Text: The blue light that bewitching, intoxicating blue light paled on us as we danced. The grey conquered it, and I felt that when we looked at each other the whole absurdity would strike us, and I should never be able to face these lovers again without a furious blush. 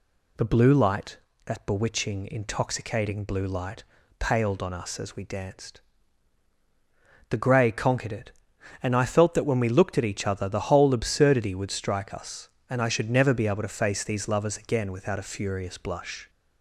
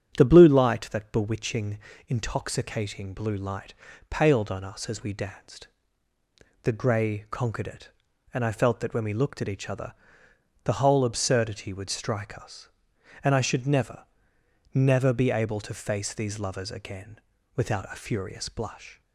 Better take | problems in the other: first | starts louder than the rest; strong; until 1.2 s; 8 dB // pauses between "light" and "paled"; slight; at 3.7 s; 0.36 s long; slight in the first // pauses between "other" and "the"; noticeable; at 9.9 s; 0.70 s long // says "never" twice; at 14.7 s // pauses between "again" and "without"; at 17.1 s; 0.38 s long

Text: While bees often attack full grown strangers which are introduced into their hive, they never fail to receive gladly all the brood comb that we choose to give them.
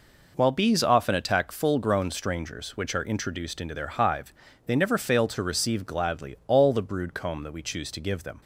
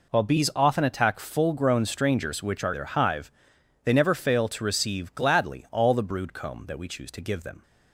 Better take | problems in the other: first | skips "introduced into"; at 2.7 s

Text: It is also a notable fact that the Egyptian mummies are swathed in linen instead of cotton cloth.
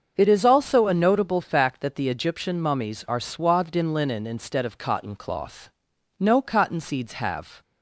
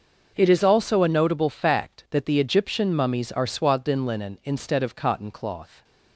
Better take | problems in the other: second | starts louder than the rest; until 1.1 s; 6.5 dB; also in the second // goes on to say "No cotton seeds have"; from 6.1 s on; 1.4 s long

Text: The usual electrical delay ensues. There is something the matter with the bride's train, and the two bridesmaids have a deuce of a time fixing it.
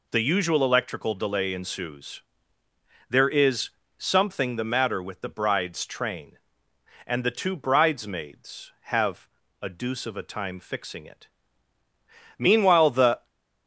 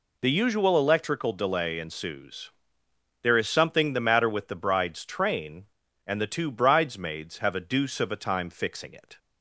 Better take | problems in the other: second | pauses between "is" and "something"; slight; at 3.6 s; 0.28 s long // pauses between "have" and "a"; slight; at 9.2 s; 0.32 s long // goes on to say "Meanwhile the"; noticeable; from 12.3 s on; 0.90 s long

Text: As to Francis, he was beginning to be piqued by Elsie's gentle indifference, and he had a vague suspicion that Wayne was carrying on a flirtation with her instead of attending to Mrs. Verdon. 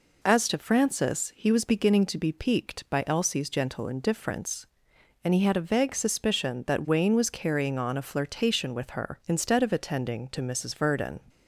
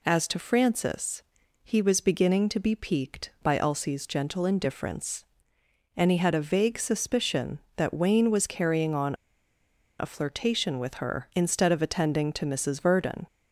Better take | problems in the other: first | pauses between "on" and "a"; noticeable; at 9.1 s; 0.85 s long

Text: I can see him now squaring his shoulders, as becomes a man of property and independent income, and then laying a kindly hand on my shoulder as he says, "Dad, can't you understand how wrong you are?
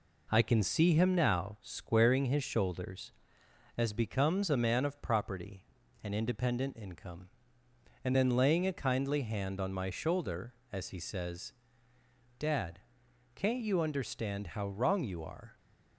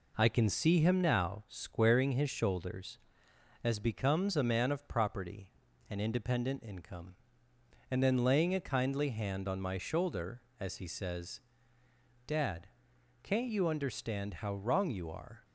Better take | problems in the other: neither | none

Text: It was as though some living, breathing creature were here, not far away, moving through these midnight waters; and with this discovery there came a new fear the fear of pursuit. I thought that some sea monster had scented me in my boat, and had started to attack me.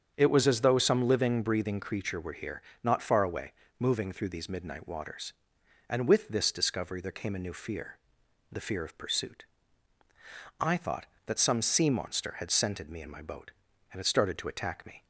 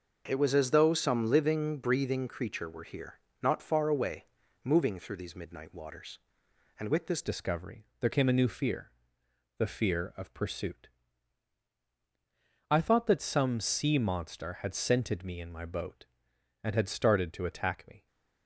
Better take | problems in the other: first | starts louder than the rest; until 1.2 s; 6 dB; strong in the first // changes voice at "discovery"; from 7.2 s on; 10.8 s long // pauses between "fear" and "the"; noticeable; at 8.9 s; 0.66 s long; noticeable in the first

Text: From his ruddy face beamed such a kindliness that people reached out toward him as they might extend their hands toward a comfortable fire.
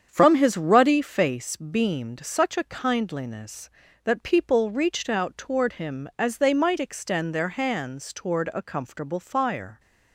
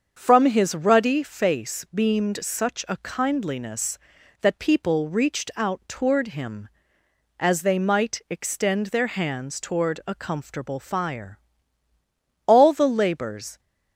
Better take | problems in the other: first | starts louder than the rest; until 1.1 s; 7 dB; strong in the first // goes on to say "All the labors"; noticeable; from 12.4 s on; 1.1 s long

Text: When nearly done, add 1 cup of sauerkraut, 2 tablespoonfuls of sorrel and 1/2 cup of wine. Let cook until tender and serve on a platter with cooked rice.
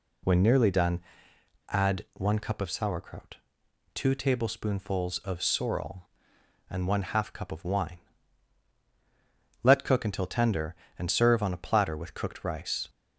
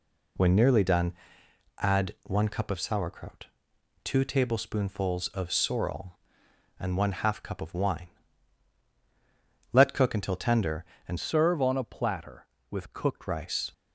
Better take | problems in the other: first | changes voice from "serve" to "cooked"; from 11.1 to 13.2 s; 2.1 s long

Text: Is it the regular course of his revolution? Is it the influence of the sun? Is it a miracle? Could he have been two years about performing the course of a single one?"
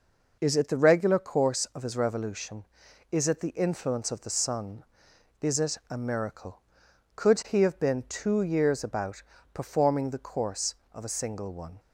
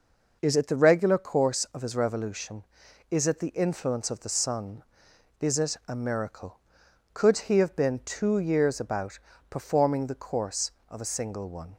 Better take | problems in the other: neither | pauses between "about" and "performing"; slight; the same in both

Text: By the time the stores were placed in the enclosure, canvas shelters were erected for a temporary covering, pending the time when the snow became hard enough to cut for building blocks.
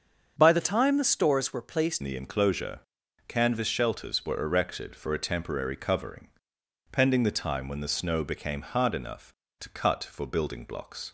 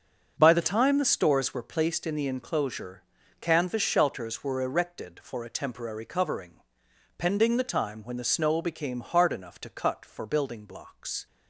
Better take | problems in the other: second | starts louder than the rest; strong; until 1.3 s; 7.5 dB; also in the second // changes voice at "in"; from 2.0 s on; 9.1 s long

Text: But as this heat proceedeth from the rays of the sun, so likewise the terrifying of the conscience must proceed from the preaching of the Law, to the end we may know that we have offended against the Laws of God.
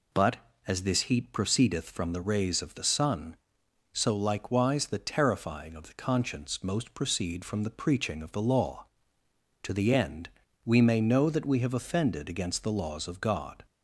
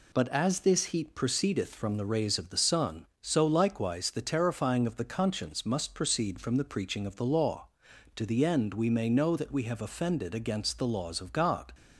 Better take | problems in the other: second | says "most" for "must"; at 6.6 s // pauses between "end" and "we"; slight; at 10.2 s; 0.36 s long

